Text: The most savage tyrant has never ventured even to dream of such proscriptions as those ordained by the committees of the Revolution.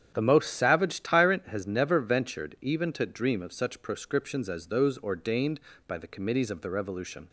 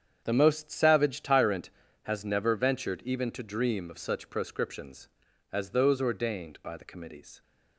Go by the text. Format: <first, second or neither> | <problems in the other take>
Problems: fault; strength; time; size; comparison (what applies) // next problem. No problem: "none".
first | starts louder than the rest; strong; until 1.2 s; 8 dB; strong in the first // stops before "of the Revolution"; at 7.4 s